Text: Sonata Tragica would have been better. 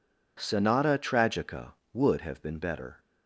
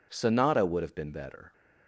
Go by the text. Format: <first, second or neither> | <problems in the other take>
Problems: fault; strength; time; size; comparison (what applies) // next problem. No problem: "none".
first | skips "Tragica"; at 0.6 s